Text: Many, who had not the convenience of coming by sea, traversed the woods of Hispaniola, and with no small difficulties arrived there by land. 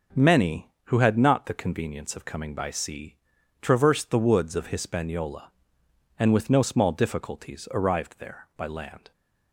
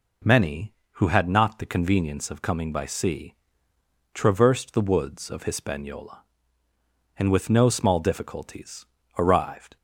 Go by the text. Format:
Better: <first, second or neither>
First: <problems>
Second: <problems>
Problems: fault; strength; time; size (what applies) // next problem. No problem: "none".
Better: first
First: none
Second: pauses between "difficulties" and "arrived"; slight; at 8.8 s; 0.31 s long // stops before "there by land"; at 9.7 s